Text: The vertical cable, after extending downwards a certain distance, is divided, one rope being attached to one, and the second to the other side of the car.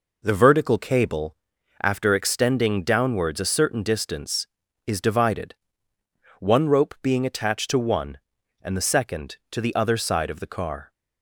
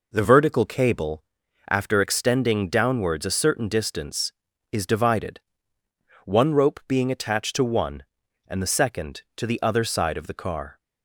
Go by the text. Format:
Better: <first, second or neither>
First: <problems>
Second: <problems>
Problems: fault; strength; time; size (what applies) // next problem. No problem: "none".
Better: neither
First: none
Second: none